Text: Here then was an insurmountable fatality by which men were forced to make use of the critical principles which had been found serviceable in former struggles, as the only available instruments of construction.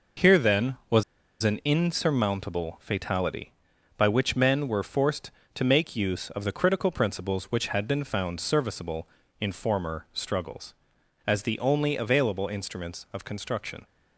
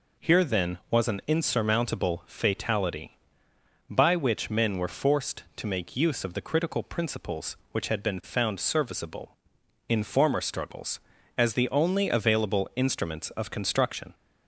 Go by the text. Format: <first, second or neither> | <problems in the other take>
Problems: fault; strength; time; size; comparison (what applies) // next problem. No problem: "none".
second | pauses between "was" and "an"; at 1.0 s; 0.39 s long